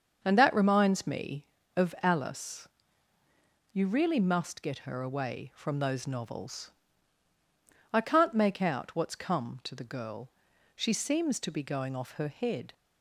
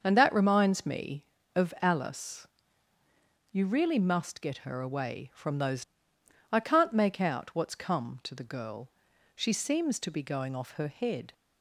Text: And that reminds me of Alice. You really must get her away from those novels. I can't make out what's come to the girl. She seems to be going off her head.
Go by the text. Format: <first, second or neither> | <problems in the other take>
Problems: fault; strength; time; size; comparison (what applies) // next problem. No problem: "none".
first | starts louder than the rest; until 1.0 s; 6.5 dB; also in the first // skips "novels"; at 6.1 s